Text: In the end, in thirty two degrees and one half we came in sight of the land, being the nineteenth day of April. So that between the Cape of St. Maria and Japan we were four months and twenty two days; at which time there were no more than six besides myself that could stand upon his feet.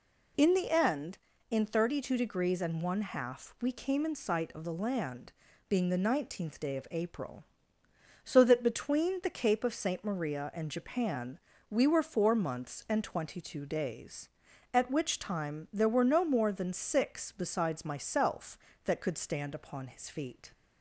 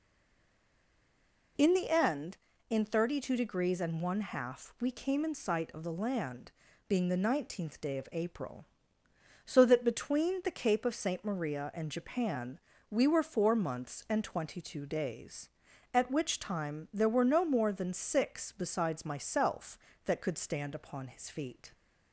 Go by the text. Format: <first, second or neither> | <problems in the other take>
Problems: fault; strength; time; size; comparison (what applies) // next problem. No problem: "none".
first | stays silent before the first word; noticeable; until 1.5 s; 1.5 s long // pauses between "Japan" and "we"; slight; at 12.5 s; 0.32 s long; slight in the first